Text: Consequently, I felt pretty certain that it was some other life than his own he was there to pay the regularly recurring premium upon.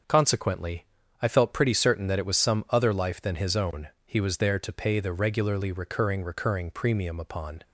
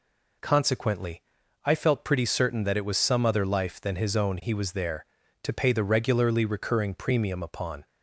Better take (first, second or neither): second